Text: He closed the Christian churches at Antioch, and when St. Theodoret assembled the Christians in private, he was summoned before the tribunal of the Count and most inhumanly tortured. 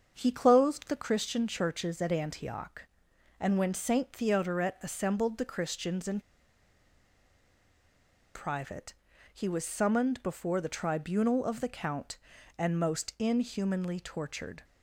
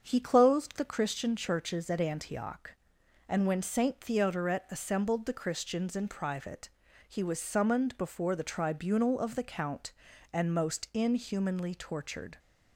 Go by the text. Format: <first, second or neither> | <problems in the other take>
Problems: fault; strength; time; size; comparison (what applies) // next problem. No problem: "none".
second | starts louder than the rest; until 1.1 s; 7 dB; also in the second // pauses between "in" and "private"; strong; at 6.2 s; 2.1 s long